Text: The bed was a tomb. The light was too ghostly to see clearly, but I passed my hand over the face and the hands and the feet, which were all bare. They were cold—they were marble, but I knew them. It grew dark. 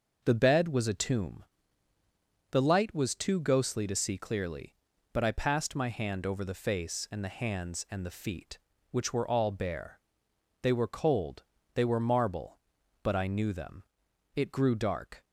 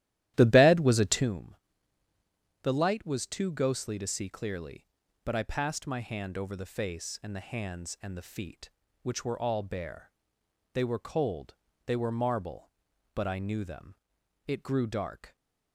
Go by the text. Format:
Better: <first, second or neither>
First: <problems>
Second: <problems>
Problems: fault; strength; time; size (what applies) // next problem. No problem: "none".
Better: first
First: none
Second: starts louder than the rest; strong; until 1.3 s; 13.5 dB